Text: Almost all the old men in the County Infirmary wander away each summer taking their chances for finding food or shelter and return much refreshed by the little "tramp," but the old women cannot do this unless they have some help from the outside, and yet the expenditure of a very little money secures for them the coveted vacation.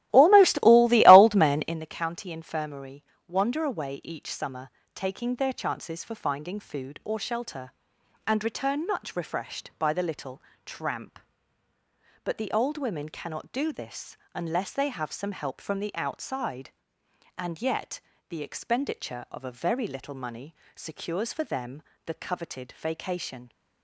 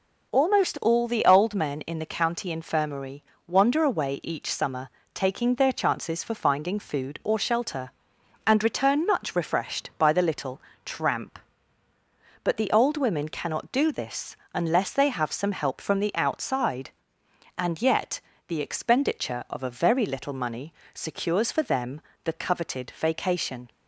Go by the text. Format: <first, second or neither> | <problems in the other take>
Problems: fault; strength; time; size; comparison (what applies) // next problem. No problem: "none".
second | starts louder than the rest; strong; until 1.8 s; 14.5 dB // pauses between "Infirmary" and "wander"; slight; at 3.0 s; 0.24 s long; slight in the second // pauses between "summer" and "taking"; slight; at 4.7 s; 0.26 s long; slight in the second // pauses between "little" and "tramp"; slight; at 10.4 s; 0.24 s long; slight in the second // pauses between "this" and "unless"; slight; at 14.1 s; 0.18 s long; slight in the second // pauses between "yet" and "the"; slight; at 17.9 s; 0.30 s long; slight in the second // pauses between "money" and "secures"; slight; at 20.5 s; 0.18 s long; slight in the second // pauses between "them" and "the"; slight; at 21.8 s; 0.22 s long; slight in the second